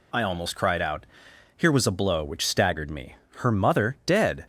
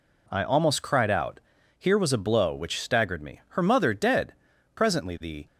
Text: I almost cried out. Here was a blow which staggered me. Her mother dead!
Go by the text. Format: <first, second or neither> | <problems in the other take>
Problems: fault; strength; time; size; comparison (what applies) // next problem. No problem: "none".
first | goes on to say "Presently the"; noticeable; from 4.7 s on; 0.70 s long